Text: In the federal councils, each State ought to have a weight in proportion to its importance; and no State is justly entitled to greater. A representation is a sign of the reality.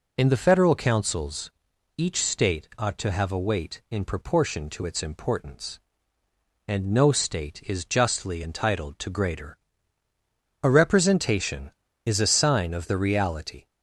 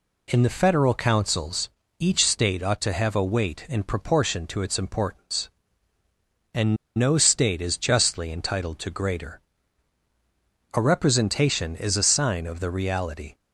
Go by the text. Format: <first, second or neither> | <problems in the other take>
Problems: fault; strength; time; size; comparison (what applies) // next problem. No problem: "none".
first | pauses between "and" and "no"; slight; at 6.7 s; 0.21 s long